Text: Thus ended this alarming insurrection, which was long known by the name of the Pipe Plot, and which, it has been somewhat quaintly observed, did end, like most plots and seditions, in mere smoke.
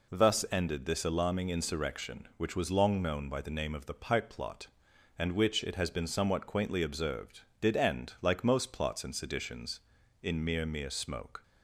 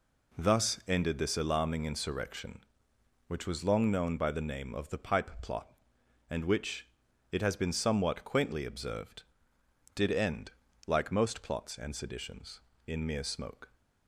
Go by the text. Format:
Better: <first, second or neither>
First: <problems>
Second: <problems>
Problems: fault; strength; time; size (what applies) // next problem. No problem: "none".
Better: second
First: says "mere" twice; at 10.6 s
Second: none